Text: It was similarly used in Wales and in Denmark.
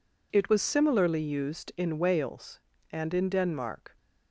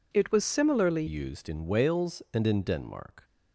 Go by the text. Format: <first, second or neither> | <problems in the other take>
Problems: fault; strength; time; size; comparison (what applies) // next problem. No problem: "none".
first | changes voice at "used"; from 1.0 s on; 2.2 s long